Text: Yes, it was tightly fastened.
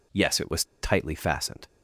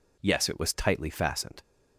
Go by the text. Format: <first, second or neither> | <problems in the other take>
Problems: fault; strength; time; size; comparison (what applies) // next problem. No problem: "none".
second | pauses between "was" and "tightly"; slight; at 0.6 s; 0.19 s long